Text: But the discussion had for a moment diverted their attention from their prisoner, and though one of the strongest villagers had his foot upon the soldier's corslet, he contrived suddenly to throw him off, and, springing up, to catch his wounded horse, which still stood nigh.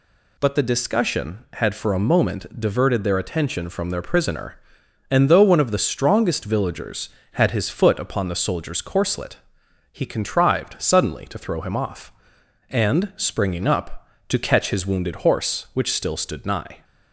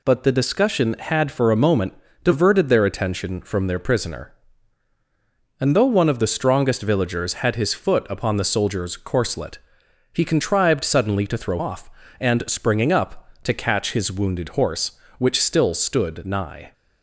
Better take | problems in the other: first | pauses between "moment" and "diverted"; slight; at 1.9 s; 0.30 s long // skips "him"; at 11.5 s

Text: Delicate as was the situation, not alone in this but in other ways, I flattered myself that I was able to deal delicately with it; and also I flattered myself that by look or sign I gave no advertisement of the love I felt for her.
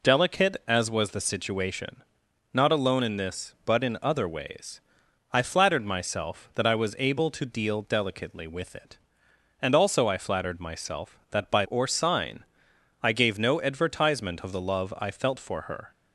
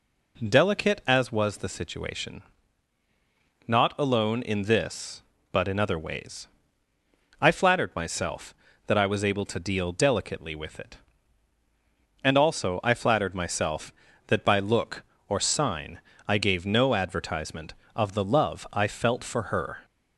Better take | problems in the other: second | skips "look"; at 11.6 s // pauses between "sign" and "I"; noticeable; at 12.4 s; 0.58 s long; slight in the second

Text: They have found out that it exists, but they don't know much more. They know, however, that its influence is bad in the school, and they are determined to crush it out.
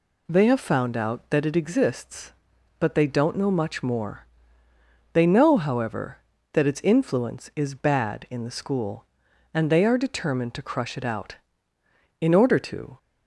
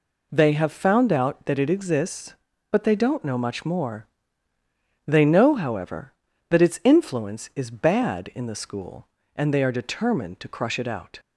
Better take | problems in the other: second | goes on to say "In order to"; noticeable; from 12.2 s on; 0.76 s long

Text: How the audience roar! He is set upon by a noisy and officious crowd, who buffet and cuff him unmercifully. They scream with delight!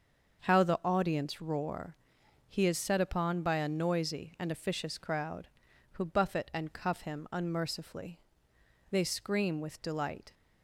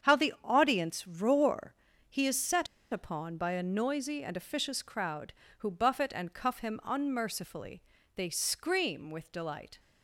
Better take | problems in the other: first | starts louder than the rest; strong; until 1.1 s; 7.5 dB; also in the first // pauses between "set" and "upon"; slight; at 2.6 s; 0.26 s long

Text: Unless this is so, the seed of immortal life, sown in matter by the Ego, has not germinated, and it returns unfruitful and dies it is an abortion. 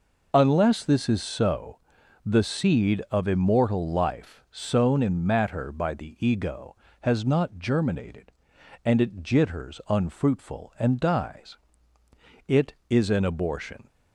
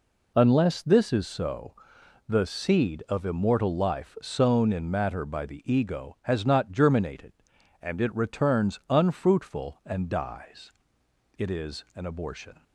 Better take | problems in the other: second | says "jitters" for "returns"; at 9.2 s // pauses between "dies" and "it"; noticeable; at 11.5 s; 0.90 s long; noticeable in the second

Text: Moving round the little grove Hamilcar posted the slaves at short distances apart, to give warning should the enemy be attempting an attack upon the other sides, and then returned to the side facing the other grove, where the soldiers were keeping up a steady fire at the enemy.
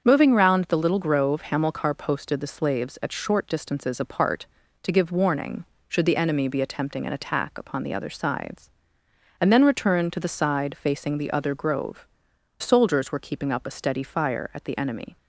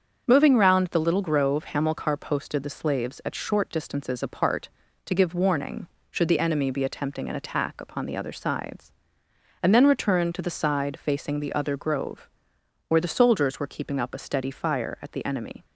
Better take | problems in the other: second | starts louder than the rest; until 1.0 s; 7 dB; also in the second // skips "where the"; at 12.3 s

